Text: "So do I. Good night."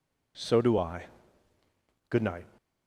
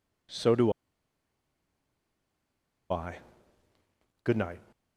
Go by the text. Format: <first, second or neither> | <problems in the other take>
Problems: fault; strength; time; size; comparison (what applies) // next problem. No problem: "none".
first | pauses between "do" and "I"; strong; at 0.7 s; 2.1 s long